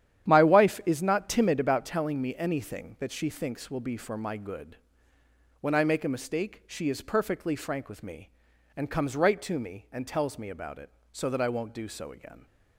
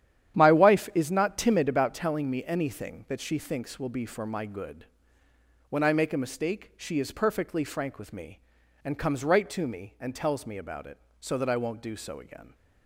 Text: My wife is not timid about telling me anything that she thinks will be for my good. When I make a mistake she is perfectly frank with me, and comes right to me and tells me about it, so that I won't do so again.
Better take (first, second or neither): neither